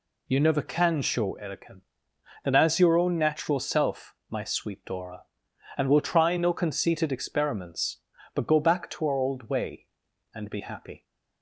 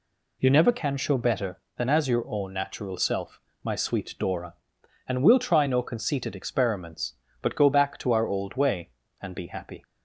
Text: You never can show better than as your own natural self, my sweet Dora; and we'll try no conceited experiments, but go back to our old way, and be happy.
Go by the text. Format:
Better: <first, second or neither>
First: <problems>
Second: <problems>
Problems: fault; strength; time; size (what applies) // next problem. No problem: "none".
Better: second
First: says "erican" for "better"; at 1.4 s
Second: none